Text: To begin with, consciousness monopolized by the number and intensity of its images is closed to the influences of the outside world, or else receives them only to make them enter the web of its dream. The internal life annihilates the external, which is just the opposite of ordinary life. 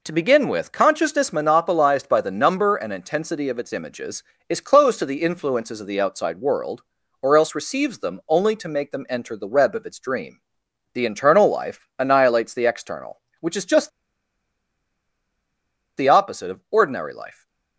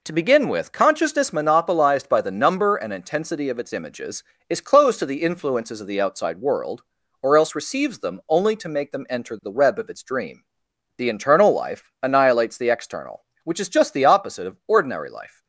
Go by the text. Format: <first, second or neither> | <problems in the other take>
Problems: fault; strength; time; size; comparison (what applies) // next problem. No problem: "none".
second | pauses between "just" and "the"; strong; at 13.8 s; 2.0 s long